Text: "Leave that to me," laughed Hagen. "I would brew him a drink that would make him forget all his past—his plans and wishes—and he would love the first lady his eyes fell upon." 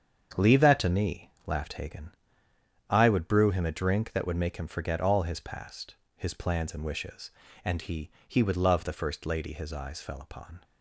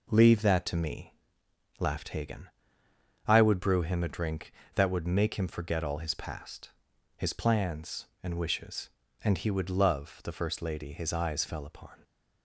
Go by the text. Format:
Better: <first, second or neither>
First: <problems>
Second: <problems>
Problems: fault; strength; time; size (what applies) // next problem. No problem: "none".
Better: second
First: starts louder than the rest; strong; until 1.5 s; 7.5 dB // says "he" twice; at 8.2 s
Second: none